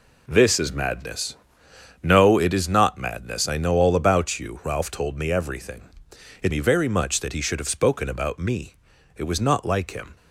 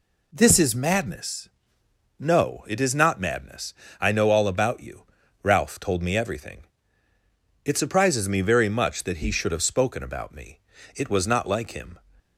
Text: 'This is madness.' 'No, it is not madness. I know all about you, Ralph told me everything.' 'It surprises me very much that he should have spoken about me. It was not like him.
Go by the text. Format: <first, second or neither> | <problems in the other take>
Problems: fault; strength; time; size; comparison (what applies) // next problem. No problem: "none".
second | skips "surprises"; at 6.5 s